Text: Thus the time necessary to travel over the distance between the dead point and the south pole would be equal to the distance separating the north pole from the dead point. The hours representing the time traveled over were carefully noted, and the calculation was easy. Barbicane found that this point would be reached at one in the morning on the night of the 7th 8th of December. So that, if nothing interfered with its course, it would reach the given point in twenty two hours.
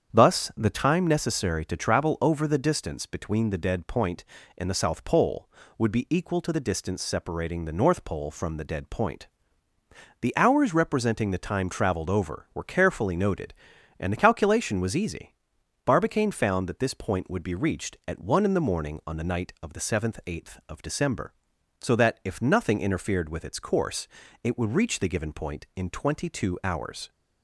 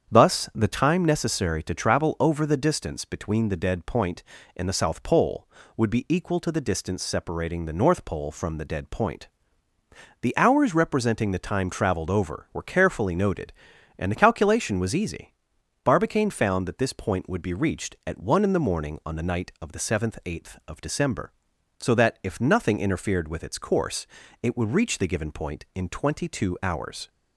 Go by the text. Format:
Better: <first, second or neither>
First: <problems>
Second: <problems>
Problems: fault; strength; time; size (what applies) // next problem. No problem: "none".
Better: neither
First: starts louder than the rest; strong; until 1.1 s; 8 dB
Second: starts louder than the rest; strong; until 1.1 s; 8 dB